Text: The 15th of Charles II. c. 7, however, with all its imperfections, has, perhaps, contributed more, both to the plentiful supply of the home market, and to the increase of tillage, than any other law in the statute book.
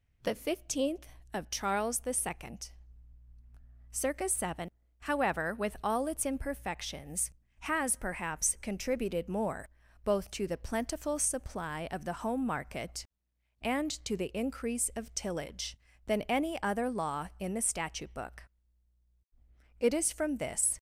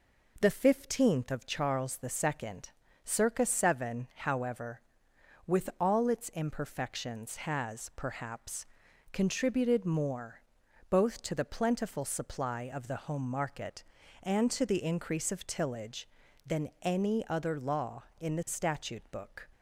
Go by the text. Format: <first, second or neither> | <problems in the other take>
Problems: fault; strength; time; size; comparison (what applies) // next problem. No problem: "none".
second | goes on to say "It is from this"; noticeable; from 19.7 s on; 1.0 s long